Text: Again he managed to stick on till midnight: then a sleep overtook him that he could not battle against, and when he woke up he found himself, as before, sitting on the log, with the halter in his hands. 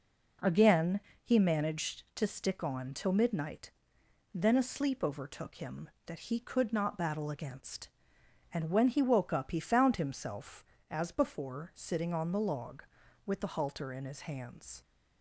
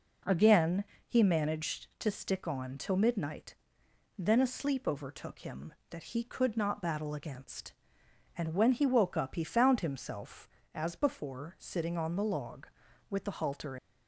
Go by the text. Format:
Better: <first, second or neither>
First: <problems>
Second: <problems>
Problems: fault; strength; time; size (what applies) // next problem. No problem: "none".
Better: first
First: pauses between "Again" and "he"; slight; at 0.9 s; 0.22 s long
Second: pauses between "Again" and "he"; slight; at 0.8 s; 0.22 s long // stops before "in his hands"; at 13.7 s